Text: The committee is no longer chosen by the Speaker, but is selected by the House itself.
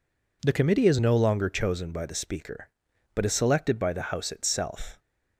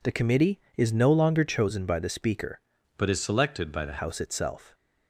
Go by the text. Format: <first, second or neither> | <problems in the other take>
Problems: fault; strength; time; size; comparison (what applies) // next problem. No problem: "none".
first | changes voice from "but" to "the"; from 2.9 to 3.9 s; 1.0 s long